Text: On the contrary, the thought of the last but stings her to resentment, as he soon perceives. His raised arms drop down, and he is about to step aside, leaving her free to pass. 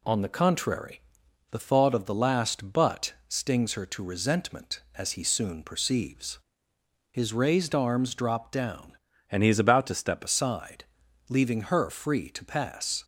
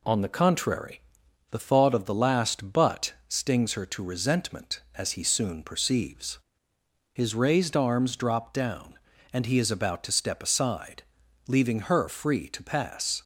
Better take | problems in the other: second | changes voice from "and" to "step"; from 9.3 to 10.2 s; 0.9 s long

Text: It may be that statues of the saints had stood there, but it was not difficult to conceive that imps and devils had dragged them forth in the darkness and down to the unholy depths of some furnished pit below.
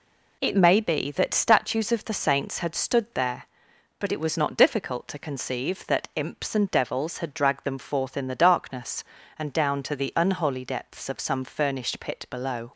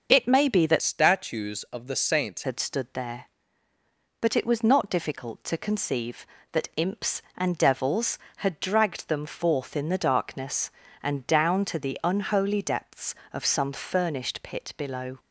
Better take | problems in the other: first | starts louder than the rest; until 1.1 s; 6.5 dB // changes voice from "statues" to "saints"; from 0.8 to 2.4 s; 1.6 s long

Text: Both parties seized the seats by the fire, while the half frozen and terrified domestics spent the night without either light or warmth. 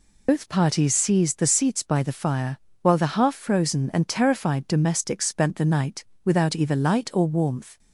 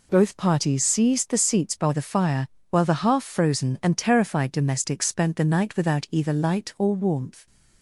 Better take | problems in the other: second | loses the start of "Both"; at 0.2 s; 60 ms // pauses between "night" and "without"; slight; at 6.0 s; 0.20 s long

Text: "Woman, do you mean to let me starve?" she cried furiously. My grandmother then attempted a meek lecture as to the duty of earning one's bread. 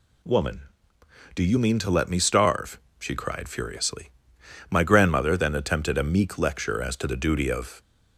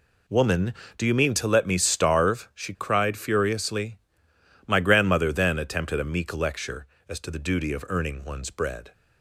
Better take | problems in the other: second | stops before "earning one's bread"; at 7.8 s

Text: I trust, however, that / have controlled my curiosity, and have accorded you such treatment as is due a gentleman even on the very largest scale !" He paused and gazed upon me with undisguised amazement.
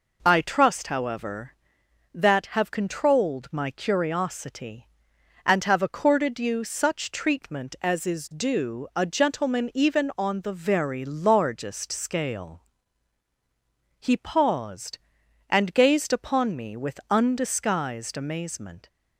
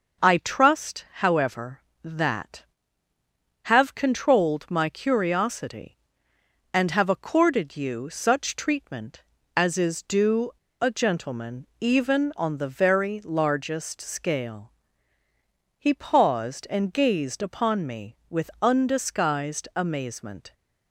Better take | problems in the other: first | pauses between "due" and "a"; slight; at 10.5 s; 0.29 s long // pauses between "gentleman" and "even"; slight; at 11.6 s; 0.16 s long

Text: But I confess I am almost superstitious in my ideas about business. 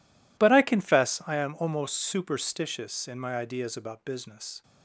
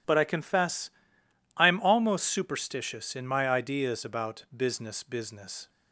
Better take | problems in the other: first | pauses between "confess" and "I"; noticeable; at 0.9 s; 0.66 s long // says "business" twice; at 5.0 s

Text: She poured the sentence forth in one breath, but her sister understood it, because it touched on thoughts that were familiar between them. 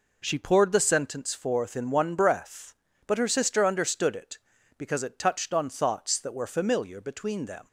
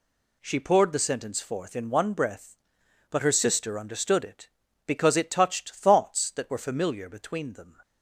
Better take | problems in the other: first | skips "on"; at 5.7 s

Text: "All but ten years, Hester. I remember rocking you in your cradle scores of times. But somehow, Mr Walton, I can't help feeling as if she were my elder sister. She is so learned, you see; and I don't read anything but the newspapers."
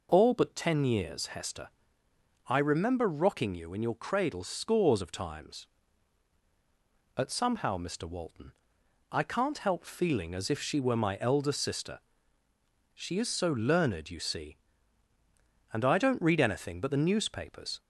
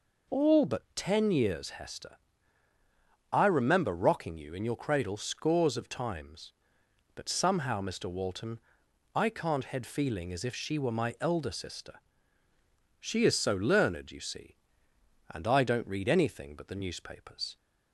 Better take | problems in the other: first | says "head" for "help"; at 9.6 s

